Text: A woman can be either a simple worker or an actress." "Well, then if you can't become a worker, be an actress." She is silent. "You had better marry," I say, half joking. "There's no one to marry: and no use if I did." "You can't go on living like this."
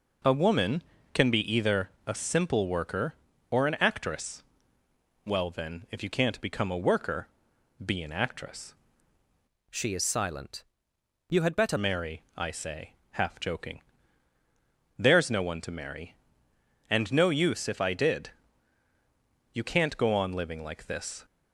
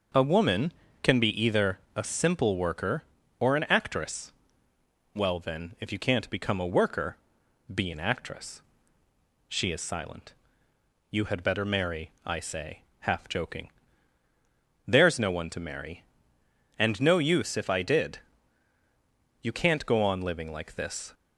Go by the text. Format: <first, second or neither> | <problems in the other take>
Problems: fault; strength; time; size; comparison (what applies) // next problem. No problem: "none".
second | pauses between "either" and "a"; slight; at 1.8 s; 0.16 s long; slight in the second // changes voice from "She" to "better"; from 9.7 to 11.7 s; 2.0 s long